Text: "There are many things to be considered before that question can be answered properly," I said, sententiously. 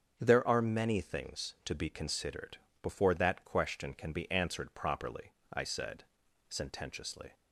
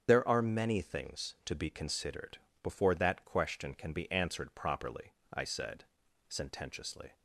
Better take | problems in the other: first | loses the start of "There"; at 0.0 s; 90 ms // starts louder than the rest; strong; until 1.0 s; 8 dB; also in the first // pauses between "considered" and "before"; slight; at 2.3 s; 0.24 s long; slight in the first

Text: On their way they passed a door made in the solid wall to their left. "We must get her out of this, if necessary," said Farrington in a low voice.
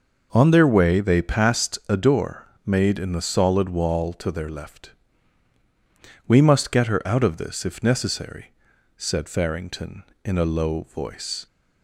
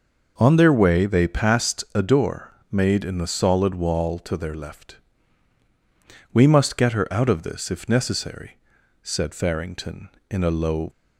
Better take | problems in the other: first | pauses between "door" and "made"; slight; at 2.5 s; 0.18 s long; slight in the first // stops before "voice"; at 10.8 s

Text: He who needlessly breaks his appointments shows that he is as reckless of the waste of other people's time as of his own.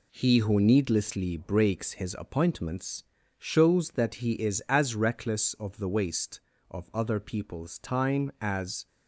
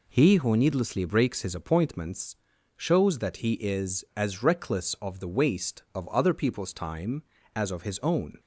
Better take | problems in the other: second | pauses between "appointments" and "shows"; slight; at 3.0 s; 0.34 s long; also in the second // stops before "of his own"; at 8.8 s

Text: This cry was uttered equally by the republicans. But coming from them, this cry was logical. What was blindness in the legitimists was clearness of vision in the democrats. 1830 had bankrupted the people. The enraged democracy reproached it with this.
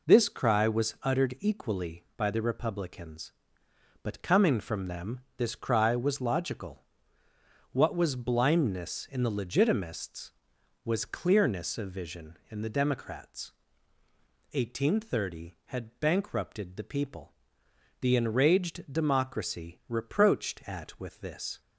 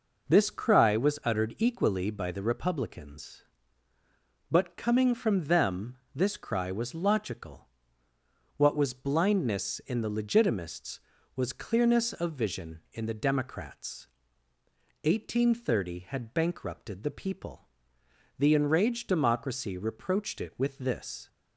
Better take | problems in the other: second | says "at" for "it"; at 20.6 s

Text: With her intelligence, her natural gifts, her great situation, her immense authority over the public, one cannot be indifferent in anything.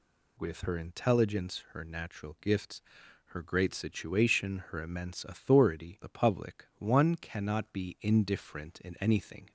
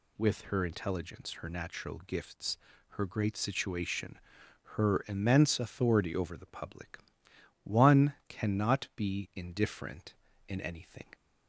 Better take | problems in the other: second | skips "over"; at 6.0 s

